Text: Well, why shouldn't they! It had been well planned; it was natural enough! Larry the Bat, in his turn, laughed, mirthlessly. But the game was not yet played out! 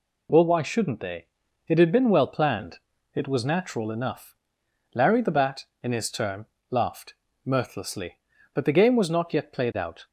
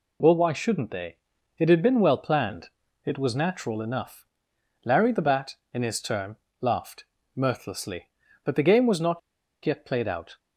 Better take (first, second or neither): first